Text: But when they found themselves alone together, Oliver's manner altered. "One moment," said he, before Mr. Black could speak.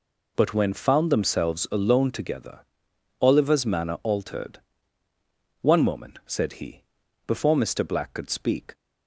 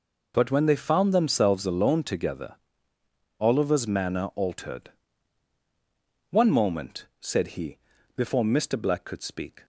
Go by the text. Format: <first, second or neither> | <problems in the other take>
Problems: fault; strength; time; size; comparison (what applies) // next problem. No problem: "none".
second | skips "they"; at 0.7 s